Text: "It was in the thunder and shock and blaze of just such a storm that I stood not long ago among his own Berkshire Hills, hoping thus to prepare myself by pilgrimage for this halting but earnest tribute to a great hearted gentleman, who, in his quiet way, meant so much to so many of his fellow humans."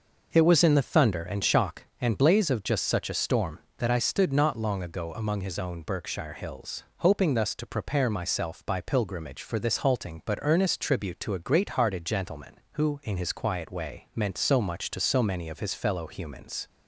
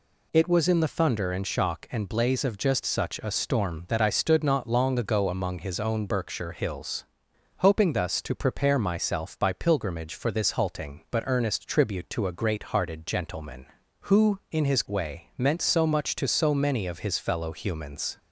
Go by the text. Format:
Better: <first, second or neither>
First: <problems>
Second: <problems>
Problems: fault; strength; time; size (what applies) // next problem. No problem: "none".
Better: first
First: none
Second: skips "quiet"; at 14.8 s